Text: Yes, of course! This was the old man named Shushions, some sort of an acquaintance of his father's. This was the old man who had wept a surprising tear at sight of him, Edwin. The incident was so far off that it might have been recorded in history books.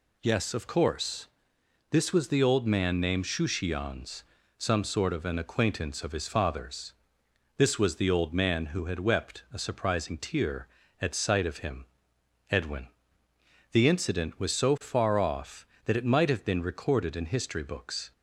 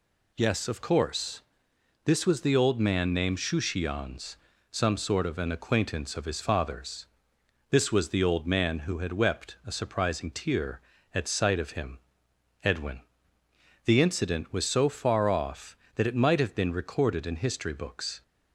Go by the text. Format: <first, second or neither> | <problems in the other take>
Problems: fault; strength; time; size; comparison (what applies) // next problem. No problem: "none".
neither | none